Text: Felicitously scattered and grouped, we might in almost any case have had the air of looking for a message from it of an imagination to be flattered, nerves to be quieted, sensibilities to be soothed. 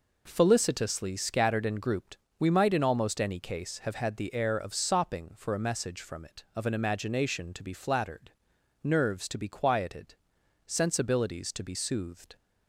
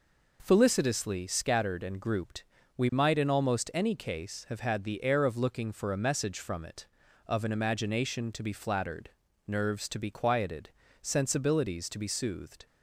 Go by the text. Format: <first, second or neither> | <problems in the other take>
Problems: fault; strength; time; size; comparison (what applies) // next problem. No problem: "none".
second | says "sopping" for "looking"; at 4.7 s